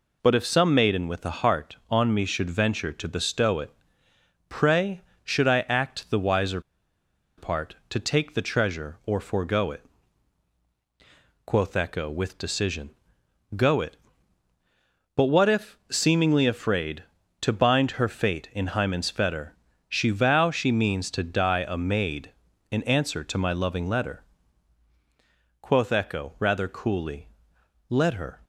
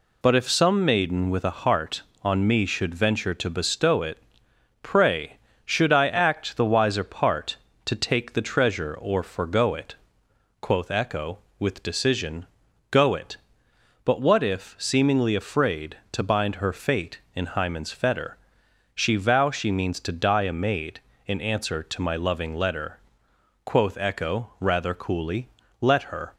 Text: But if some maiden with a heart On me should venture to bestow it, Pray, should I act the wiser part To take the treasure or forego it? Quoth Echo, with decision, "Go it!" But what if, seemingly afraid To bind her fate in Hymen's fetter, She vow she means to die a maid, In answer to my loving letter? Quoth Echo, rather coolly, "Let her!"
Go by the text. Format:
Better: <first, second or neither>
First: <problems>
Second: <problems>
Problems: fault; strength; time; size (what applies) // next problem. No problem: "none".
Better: second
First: pauses between "wiser" and "part"; noticeable; at 6.5 s; 0.78 s long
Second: none